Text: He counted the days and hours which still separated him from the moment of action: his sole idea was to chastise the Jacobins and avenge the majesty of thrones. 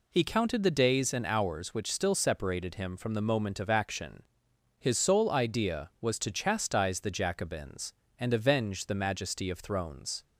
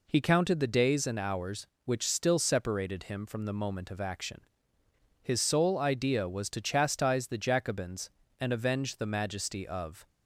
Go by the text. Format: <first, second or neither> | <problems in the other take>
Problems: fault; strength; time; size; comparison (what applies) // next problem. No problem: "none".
first | stops before "thrones"; at 10.0 s